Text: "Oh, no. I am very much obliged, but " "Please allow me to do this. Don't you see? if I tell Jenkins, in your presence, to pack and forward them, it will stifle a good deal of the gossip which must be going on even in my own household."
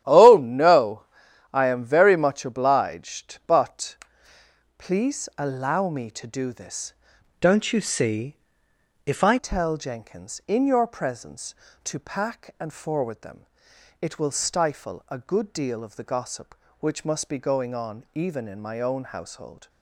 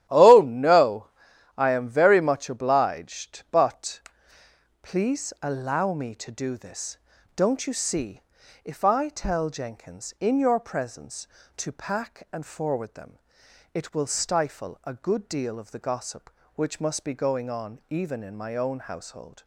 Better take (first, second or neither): second